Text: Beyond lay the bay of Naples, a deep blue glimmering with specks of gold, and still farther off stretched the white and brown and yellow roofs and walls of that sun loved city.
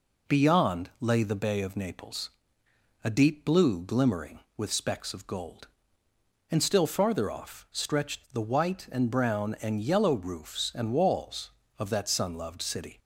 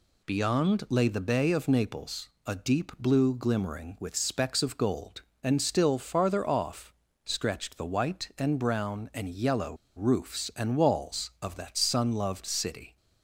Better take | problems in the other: first | pauses between "off" and "stretched"; slight; at 6.9 s; 0.32 s long // pauses between "yellow" and "roofs"; slight; at 9.7 s; 0.21 s long

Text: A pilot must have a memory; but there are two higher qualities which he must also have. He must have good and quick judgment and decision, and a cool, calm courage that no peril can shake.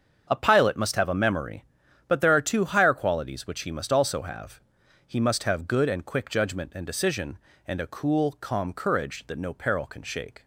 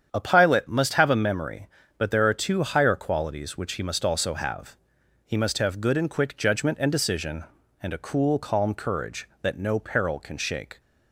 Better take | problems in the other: neither | starts louder than the rest; strong; the same in both

